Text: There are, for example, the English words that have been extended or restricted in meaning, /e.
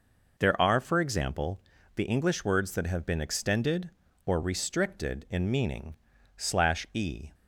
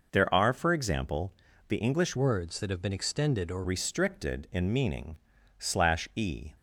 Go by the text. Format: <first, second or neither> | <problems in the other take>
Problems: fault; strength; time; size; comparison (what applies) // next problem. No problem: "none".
first | changes voice from "words" to "or"; from 2.1 to 3.6 s; 1.5 s long